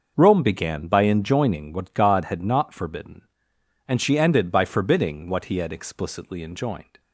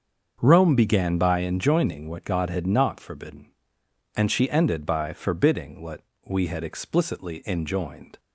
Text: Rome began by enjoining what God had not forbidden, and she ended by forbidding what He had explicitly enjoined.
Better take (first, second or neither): first